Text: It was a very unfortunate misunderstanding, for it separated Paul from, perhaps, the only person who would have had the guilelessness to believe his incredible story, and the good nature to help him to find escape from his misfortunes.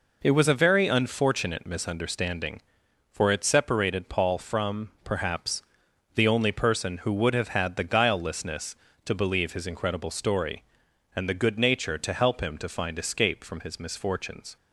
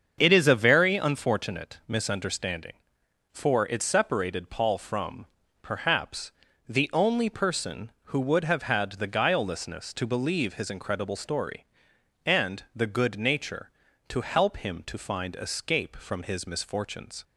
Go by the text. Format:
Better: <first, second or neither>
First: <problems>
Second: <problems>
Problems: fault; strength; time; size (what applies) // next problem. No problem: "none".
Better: first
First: none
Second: starts louder than the rest; strong; until 1.2 s; 7 dB // says "is" for "was"; at 0.3 s